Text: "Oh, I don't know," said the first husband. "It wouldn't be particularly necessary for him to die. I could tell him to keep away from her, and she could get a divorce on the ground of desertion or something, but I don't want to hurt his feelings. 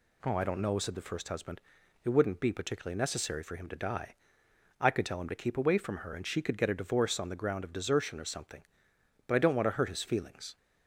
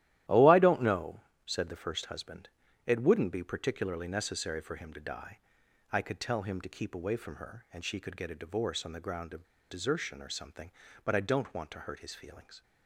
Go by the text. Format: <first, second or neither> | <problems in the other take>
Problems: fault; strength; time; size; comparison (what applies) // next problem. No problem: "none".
first | starts louder than the rest; strong; until 1.5 s; 13.5 dB // pauses between "of" and "desertion"; slight; at 9.4 s; 0.25 s long